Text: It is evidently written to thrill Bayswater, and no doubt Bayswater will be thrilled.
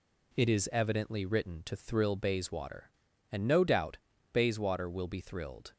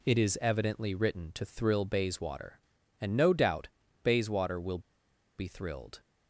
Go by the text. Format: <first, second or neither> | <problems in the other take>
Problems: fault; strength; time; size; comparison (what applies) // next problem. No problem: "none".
first | pauses between "doubt" and "Bayswater"; slight; at 3.6 s; 0.34 s long; slight in the first // pauses between "will" and "be"; noticeable; at 4.7 s; 0.59 s long